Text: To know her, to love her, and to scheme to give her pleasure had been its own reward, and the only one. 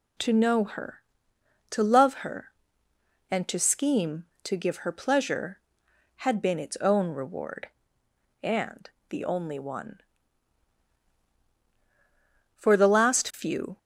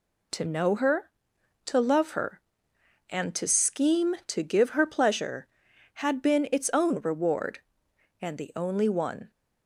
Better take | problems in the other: second | pauses between "and" and "the"; slight; at 8.8 s; 0.20 s long // goes on to say "For the last few"; noticeable; from 12.5 s on; 1.1 s long

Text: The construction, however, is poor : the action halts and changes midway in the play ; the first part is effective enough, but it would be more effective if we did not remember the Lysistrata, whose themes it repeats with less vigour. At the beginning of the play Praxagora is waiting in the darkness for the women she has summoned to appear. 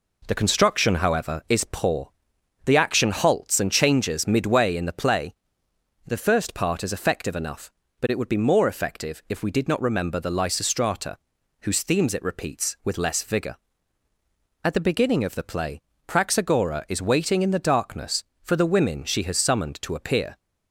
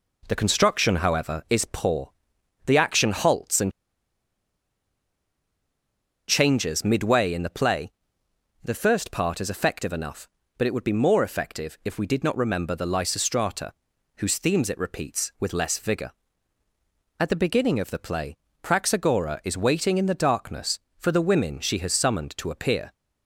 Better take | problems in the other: first | pauses between "and" and "changes"; strong; at 3.6 s; 2.5 s long // pauses between "play" and "Praxagora"; slight; at 18.3 s; 0.24 s long; slight in the first

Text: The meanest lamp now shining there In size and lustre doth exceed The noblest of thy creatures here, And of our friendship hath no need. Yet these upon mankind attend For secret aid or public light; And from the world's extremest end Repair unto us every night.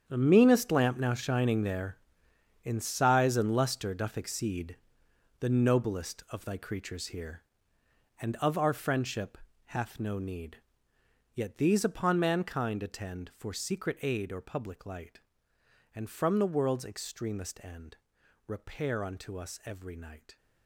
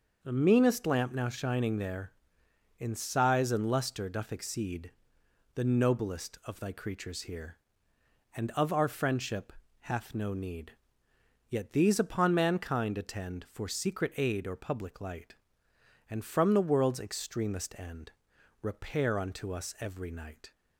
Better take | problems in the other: second | gets quieter; strong; throughout; 13.5 dB // pauses between "exceed" and "The"; noticeable; at 4.7 s; 0.64 s long; noticeable in the second // pauses between "friendship" and "hath"; slight; at 9.3 s; 0.34 s long; slight in the second // pauses between "end" and "Repair"; noticeable; at 17.9 s; 0.50 s long; noticeable in the second

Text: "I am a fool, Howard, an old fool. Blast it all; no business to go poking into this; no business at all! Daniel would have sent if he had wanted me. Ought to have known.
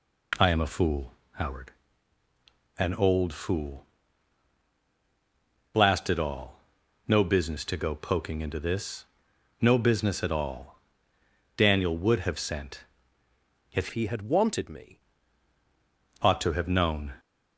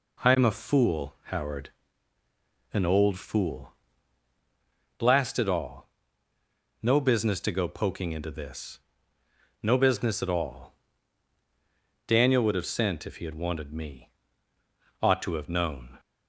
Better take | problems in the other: second | pauses between "sent" and "if"; noticeable; at 12.7 s; 0.94 s long // changes voice from "he" to "me"; from 13.9 to 14.9 s; 1.0 s long

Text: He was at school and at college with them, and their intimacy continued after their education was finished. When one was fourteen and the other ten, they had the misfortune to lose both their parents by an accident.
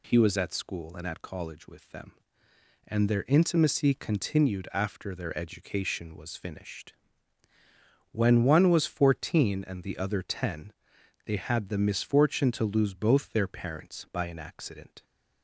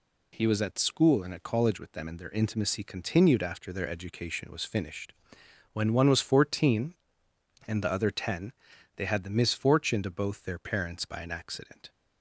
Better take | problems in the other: first | skips "lose"; at 10.1 s

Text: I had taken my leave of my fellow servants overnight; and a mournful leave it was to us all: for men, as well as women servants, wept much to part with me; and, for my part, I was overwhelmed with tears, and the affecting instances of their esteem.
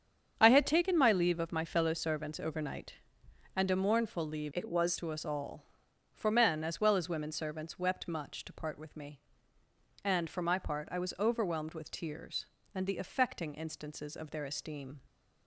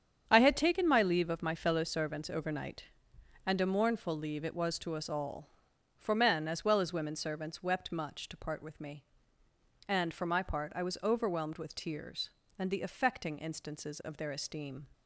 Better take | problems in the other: second | starts louder than the rest; strong; until 1.3 s; 8 dB; strong in the second // changes voice from "it" to "was"; from 4.5 to 4.9 s; 0.4 s long

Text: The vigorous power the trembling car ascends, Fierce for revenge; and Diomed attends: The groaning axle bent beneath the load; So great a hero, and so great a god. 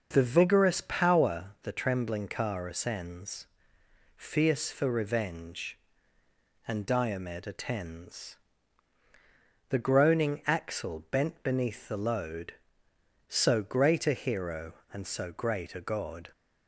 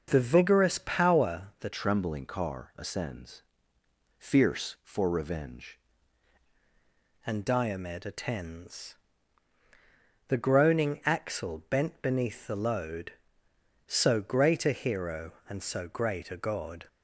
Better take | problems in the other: first | starts louder than the rest; until 1.1 s; 6 dB; also in the first // changes voice from "trembling" to "revenge"; from 1.7 to 5.7 s; 4.0 s long

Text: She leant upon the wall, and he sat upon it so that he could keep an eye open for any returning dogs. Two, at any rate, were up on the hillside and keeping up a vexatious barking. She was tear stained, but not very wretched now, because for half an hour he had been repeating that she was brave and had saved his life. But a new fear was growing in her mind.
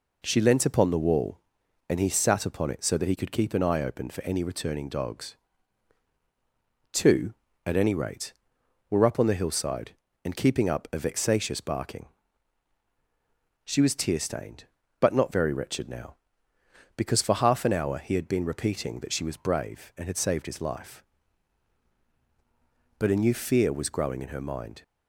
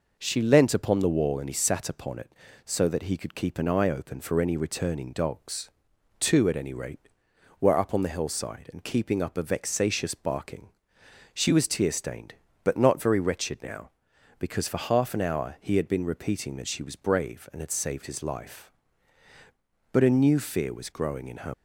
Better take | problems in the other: first | stops before "mind"; at 21.5 s

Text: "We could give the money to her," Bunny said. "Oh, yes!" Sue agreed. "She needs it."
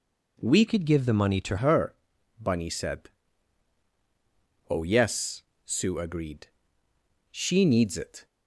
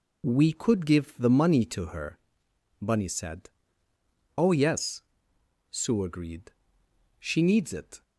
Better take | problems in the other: second | changes voice from "could" to "to"; from 0.6 to 1.5 s; 0.9 s long

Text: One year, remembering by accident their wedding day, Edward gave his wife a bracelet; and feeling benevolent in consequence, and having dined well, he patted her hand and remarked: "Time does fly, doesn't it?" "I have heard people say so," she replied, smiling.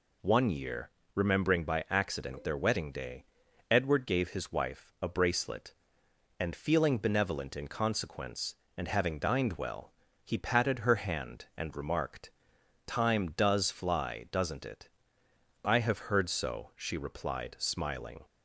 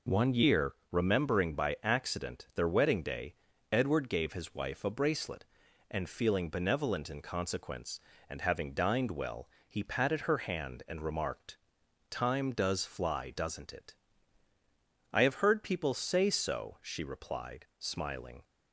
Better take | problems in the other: second | skips "people say"; at 16.2 s

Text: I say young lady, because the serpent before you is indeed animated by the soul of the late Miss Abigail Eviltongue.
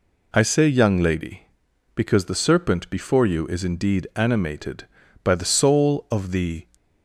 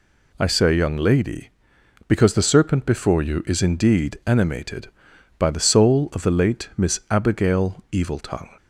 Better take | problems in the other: second | stops before "late Miss Abigail Eviltongue"; at 6.7 s

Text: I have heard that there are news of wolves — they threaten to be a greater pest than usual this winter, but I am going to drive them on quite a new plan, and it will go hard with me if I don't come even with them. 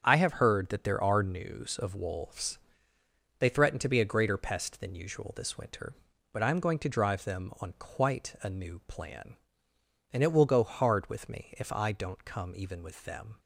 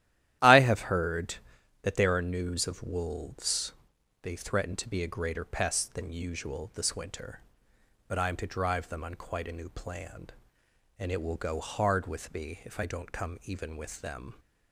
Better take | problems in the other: first | starts louder than the rest; strong; until 1.8 s; 12.5 dB; also in the first // skips "going"; at 8.3 s

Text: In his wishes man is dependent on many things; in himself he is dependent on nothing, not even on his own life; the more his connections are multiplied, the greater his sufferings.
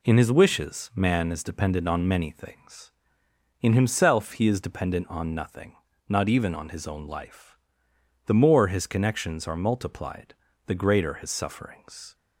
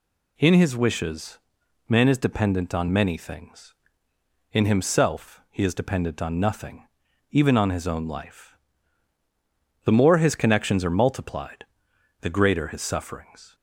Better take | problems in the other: first | pauses between "wishes" and "man"; noticeable; at 1.3 s; 0.50 s long // skips "not"; at 7.0 s

